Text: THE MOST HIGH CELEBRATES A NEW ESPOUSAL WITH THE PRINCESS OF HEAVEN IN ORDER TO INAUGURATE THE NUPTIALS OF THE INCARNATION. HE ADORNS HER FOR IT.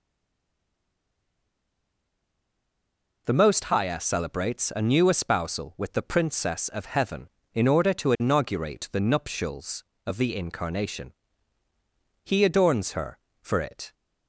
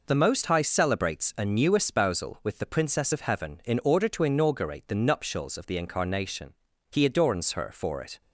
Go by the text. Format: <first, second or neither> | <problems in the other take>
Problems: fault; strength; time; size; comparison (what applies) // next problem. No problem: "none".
second | stays silent before the first word; strong; until 3.2 s; 3.2 s long